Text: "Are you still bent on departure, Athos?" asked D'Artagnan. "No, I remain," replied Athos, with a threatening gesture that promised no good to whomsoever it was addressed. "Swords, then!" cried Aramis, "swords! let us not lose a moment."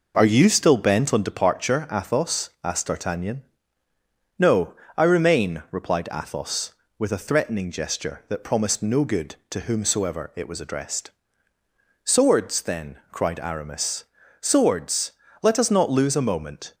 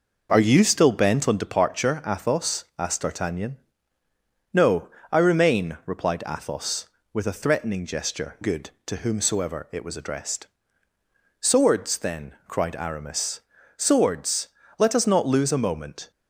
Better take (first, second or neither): first